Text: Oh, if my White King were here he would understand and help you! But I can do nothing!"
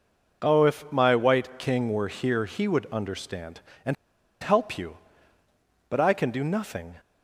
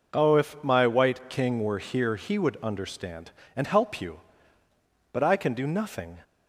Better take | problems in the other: second | pauses between "and" and "help"; noticeable; at 3.9 s; 0.47 s long

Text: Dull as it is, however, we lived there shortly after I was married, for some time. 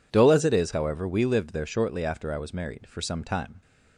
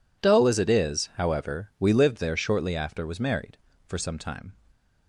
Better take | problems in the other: first | skips "I"; at 3.0 s

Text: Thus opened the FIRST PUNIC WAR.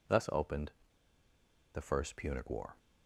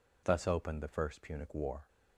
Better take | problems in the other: second | pauses between "opened" and "the"; at 0.7 s; 1.0 s long

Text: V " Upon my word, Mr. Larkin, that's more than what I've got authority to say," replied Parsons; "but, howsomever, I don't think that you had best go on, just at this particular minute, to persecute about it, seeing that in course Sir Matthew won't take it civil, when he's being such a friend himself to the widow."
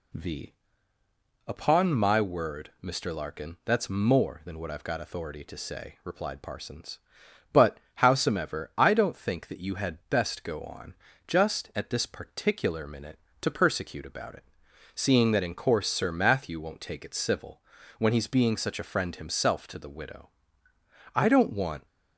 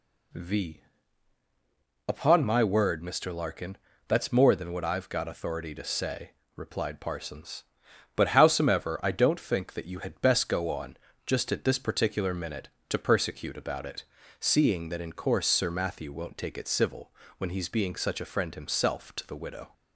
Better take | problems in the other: second | goes on to say "I don't want"; noticeable; from 21.1 s on; 0.70 s long

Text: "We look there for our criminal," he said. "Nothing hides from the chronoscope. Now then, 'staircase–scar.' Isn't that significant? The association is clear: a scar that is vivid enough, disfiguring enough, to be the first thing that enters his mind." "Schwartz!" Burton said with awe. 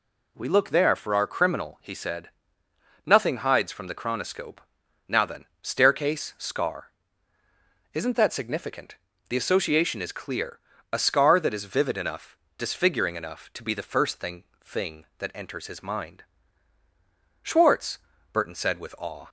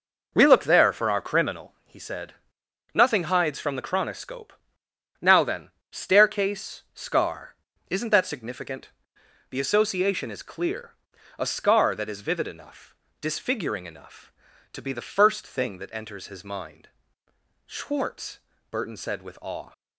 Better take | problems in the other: second | says "thing" twice; at 14.6 s

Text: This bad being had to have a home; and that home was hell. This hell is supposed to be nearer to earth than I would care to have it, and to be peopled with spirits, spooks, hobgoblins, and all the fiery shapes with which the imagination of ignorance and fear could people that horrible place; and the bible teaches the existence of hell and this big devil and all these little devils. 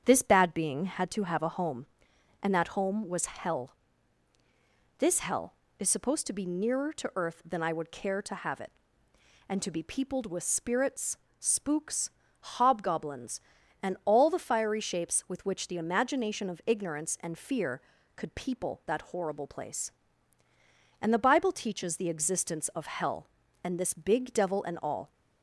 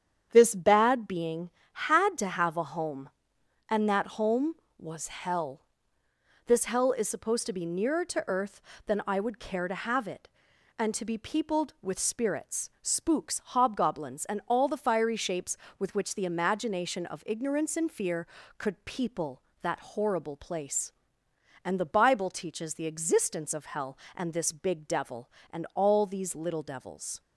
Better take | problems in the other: second | starts louder than the rest; strong; until 1.0 s; 8 dB; strong in the second // stops before "these little devils"; at 25.1 s

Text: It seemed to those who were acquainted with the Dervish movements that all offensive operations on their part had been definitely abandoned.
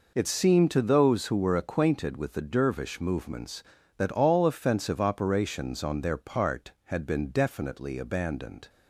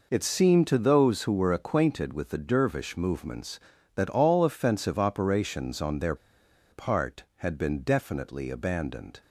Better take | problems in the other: first | pauses between "their" and "part"; noticeable; at 6.1 s; 0.56 s long

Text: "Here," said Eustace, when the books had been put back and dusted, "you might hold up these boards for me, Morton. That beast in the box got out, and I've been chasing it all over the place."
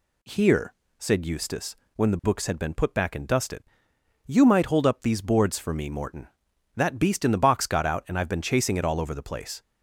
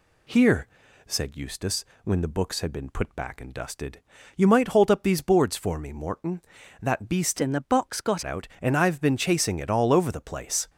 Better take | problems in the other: first | changes voice from "in" to "got"; from 7.4 to 8.2 s; 0.8 s long

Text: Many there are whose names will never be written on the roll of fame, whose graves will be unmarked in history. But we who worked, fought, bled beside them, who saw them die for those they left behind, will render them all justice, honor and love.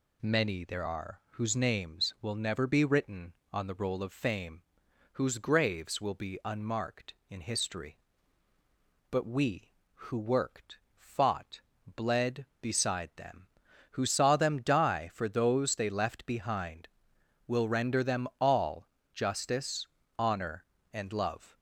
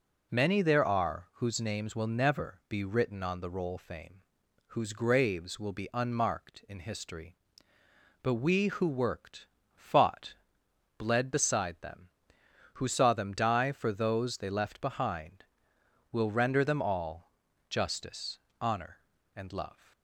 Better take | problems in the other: first | skips "of"; at 3.7 s // pauses between "all" and "justice"; at 17.3 s; 0.38 s long; slight in the first

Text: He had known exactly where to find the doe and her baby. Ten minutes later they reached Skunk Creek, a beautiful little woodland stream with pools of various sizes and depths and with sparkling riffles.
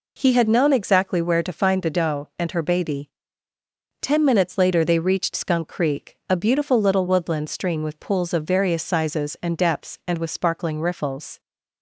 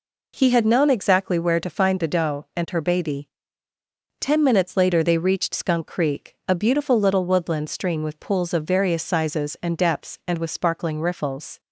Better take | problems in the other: neither | none

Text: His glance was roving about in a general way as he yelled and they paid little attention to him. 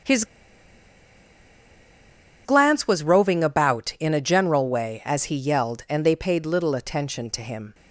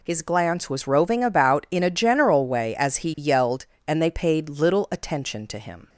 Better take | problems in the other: second | starts louder than the rest; strong; until 3.2 s; 7.5 dB // pauses between "His" and "glance"; strong; at 0.2 s; 2.2 s long

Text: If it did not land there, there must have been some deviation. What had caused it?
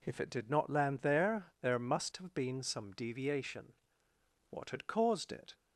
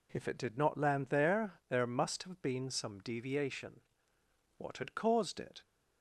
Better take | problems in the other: neither | none

